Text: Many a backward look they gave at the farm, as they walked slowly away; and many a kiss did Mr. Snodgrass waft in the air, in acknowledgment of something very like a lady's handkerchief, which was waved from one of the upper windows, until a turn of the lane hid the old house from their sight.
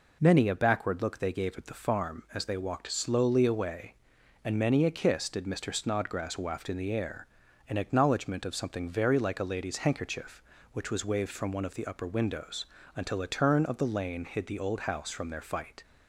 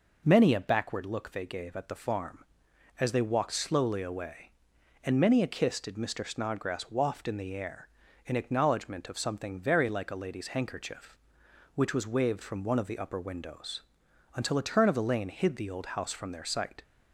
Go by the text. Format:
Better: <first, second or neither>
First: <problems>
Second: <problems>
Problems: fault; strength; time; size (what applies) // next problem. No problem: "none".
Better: second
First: says "fight" for "sight"; at 15.4 s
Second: none